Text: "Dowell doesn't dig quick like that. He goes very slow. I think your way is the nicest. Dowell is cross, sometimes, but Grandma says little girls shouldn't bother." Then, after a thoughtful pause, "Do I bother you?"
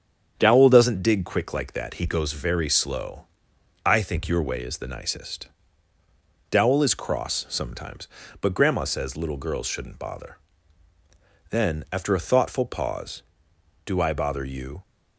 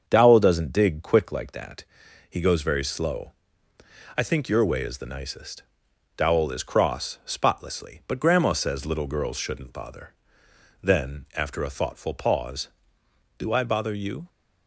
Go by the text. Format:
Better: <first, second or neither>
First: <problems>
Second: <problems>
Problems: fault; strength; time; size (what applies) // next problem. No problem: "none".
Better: first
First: starts louder than the rest; strong; until 1.3 s; 8 dB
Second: starts louder than the rest; until 1.0 s; 7 dB // says "spotlessly" for "sometimes"; at 7.2 s